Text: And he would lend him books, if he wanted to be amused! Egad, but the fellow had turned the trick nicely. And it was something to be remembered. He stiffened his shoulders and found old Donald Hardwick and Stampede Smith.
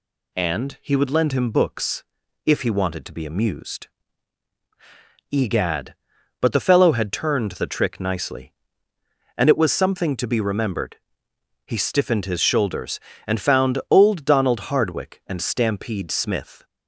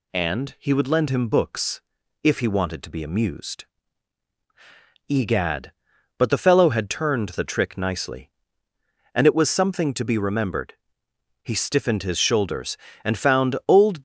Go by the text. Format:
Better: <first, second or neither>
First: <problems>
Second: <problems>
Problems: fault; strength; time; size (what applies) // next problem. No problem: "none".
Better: first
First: none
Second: stops before "Donald Hardwick and Stampede Smith"; at 13.9 s